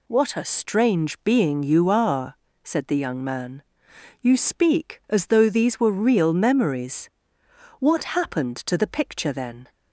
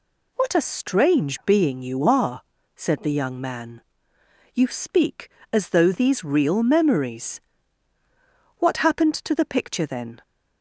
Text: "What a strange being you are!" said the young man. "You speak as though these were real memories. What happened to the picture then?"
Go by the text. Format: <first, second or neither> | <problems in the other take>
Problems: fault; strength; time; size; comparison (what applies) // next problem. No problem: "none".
first | skips "were"; at 6.2 s